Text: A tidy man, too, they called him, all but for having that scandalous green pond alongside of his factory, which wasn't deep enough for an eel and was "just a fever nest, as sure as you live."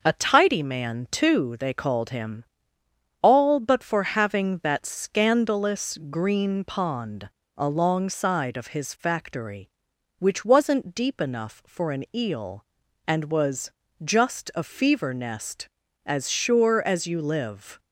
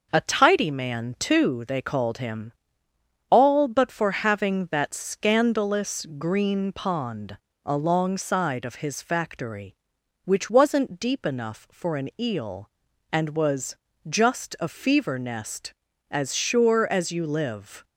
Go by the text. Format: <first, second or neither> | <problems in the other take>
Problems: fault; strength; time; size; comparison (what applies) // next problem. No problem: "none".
neither | pauses between "pond" and "alongside"; slight; the same in both // pauses between "was" and "just"; slight; the same in both